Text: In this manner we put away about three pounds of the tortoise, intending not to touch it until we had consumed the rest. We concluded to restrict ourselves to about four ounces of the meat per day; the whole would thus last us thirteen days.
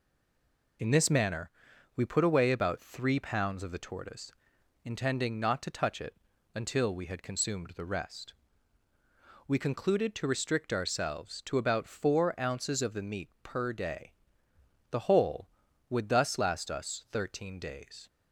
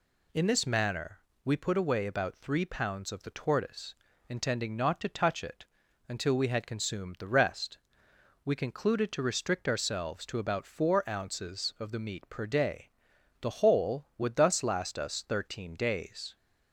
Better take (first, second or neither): second